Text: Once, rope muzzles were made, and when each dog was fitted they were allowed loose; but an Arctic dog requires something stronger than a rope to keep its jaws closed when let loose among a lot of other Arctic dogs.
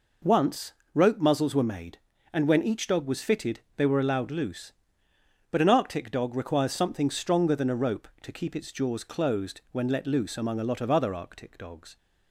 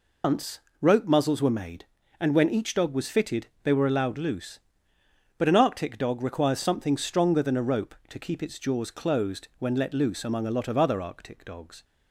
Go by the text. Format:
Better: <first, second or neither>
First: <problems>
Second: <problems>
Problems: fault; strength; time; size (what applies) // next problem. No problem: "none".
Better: first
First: pauses between "fitted" and "they"; slight; at 3.5 s; 0.16 s long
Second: loses the start of "Once"; at 0.2 s; 155 ms // pauses between "fitted" and "they"; slight; at 3.4 s; 0.16 s long